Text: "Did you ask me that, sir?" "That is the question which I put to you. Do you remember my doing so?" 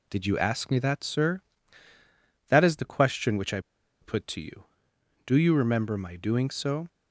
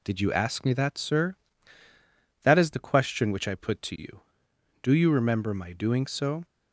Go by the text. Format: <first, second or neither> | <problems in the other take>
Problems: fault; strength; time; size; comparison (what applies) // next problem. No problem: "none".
second | pauses between "I" and "put"; at 3.5 s; 0.42 s long